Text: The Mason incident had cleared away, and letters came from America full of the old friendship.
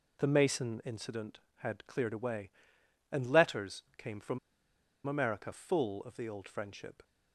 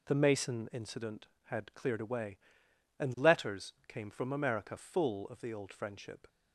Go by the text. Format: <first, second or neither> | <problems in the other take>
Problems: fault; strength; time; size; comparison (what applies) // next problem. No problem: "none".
second | pauses between "from" and "America"; noticeable; at 4.3 s; 0.68 s long